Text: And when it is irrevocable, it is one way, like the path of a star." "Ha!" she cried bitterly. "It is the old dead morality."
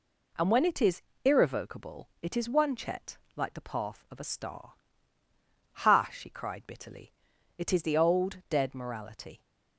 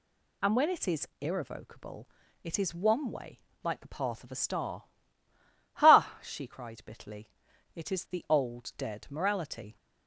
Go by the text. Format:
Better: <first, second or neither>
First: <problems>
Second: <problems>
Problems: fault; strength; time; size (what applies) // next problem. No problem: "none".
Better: second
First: pauses between "is" and "irrevocable"; slight; at 1.0 s; 0.22 s long // says "chet" for "way"; at 2.7 s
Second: none